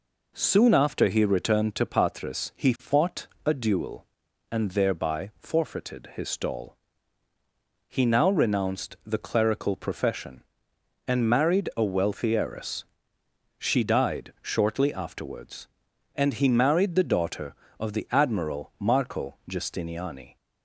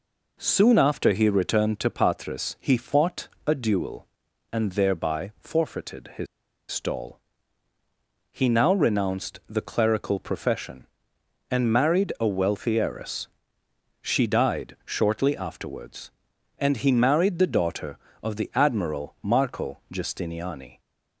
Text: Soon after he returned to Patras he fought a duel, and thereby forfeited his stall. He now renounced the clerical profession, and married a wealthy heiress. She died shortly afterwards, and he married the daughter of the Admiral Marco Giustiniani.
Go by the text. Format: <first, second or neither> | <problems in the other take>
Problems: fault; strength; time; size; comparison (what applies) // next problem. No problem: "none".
first | pauses between "fought" and "a"; slight; at 3.2 s; 0.20 s long; slight in the first // pauses between "his" and "stall"; at 6.2 s; 0.45 s long